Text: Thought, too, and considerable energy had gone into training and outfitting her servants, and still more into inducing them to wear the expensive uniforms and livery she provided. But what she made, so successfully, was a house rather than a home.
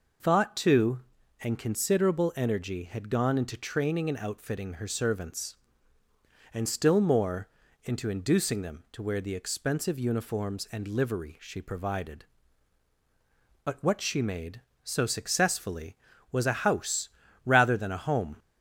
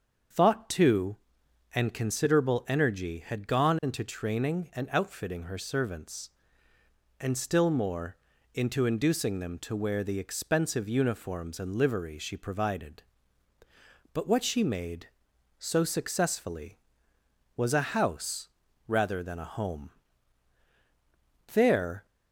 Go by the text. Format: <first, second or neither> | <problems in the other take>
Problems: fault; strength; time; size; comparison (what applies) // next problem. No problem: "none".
first | starts louder than the rest; until 1.9 s; 7 dB // pauses between "more" and "into"; slight; at 8.1 s; 0.36 s long; slight in the first // pauses between "house" and "rather"; at 18.4 s; 0.40 s long; also in the first // goes on to say "There"; from 21.5 s on; 0.52 s long